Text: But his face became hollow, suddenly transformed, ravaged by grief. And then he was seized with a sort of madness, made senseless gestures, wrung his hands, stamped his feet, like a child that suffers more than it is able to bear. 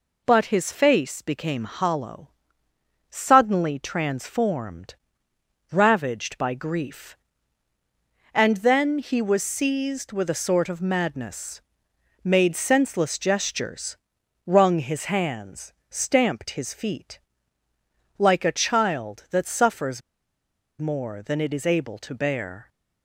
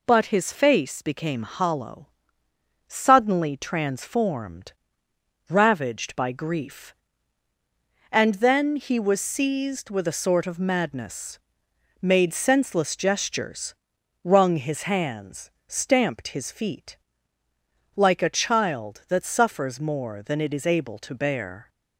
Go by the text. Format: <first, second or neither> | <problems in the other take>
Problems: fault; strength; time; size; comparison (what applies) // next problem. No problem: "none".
second | pauses between "suffers" and "more"; noticeable; at 20.0 s; 0.79 s long